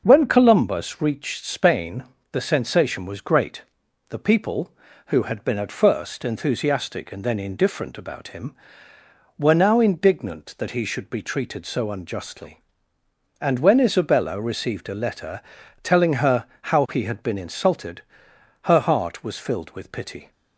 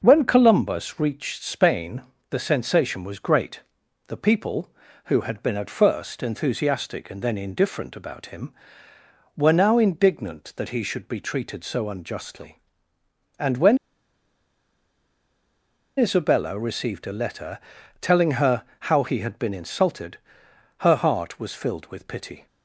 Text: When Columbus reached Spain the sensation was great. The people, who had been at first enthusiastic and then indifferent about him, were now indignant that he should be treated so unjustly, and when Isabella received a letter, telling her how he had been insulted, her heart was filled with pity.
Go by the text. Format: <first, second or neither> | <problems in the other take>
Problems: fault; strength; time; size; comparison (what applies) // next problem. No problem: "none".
first | pauses between "Spain" and "the"; slight; at 2.0 s; 0.28 s long; slight in the first // pauses between "when" and "Isabella"; strong; at 13.7 s; 2.2 s long // pauses between "her" and "how"; slight; at 18.6 s; 0.24 s long; slight in the first